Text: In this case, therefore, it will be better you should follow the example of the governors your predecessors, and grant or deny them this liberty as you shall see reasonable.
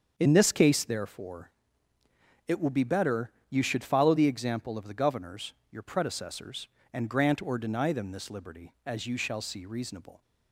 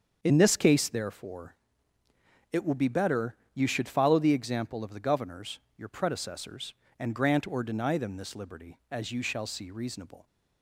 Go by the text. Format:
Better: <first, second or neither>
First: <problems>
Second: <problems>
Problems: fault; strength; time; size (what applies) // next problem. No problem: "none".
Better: neither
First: starts louder than the rest; until 1.1 s; 7 dB // pauses between "better" and "you"; slight; at 3.3 s; 0.20 s long // pauses between "governors" and "your"; slight; at 5.5 s; 0.20 s long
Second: starts louder than the rest; until 1.2 s; 7 dB // pauses between "better" and "you"; slight; at 3.3 s; 0.20 s long // pauses between "governors" and "your"; slight; at 5.5 s; 0.20 s long